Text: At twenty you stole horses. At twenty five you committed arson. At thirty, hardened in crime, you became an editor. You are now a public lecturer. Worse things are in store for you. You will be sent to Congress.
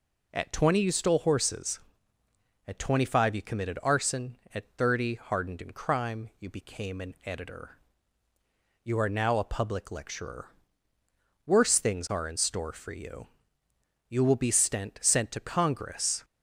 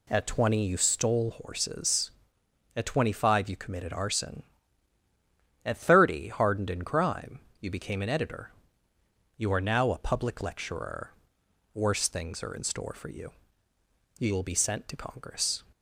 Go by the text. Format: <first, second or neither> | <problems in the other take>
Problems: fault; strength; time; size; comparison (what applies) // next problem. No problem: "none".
second | says "sent" twice; at 15.0 s